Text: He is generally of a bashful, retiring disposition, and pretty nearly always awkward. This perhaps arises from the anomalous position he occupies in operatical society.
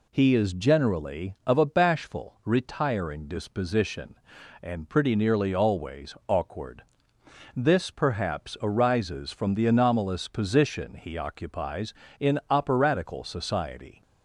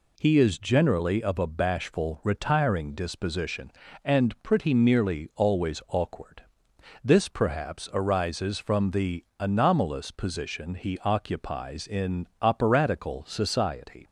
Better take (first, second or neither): neither